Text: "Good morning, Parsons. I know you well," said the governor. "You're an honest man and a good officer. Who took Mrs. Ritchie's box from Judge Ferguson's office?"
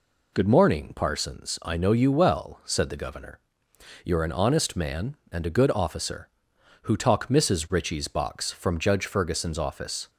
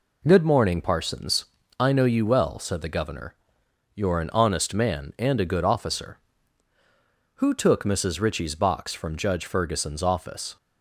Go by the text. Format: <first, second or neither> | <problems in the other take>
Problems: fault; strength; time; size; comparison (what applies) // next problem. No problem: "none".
second | says "talk" for "took"; at 6.9 s